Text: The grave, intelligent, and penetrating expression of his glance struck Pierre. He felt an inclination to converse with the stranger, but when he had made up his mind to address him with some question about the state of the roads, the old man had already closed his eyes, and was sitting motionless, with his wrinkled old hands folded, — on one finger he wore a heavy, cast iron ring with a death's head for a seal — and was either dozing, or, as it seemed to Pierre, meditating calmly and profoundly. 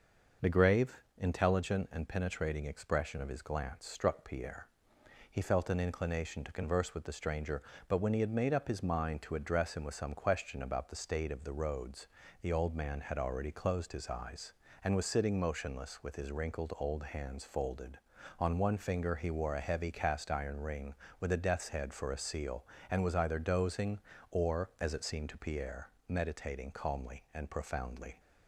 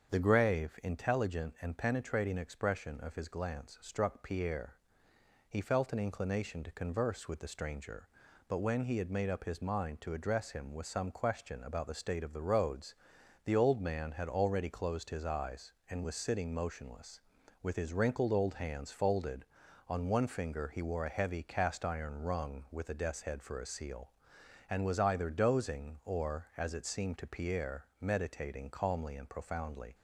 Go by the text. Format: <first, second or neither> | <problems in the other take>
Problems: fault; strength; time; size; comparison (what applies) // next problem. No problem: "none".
first | starts louder than the rest; strong; until 1.1 s; 7 dB // says "rung" for "ring"; at 22.2 s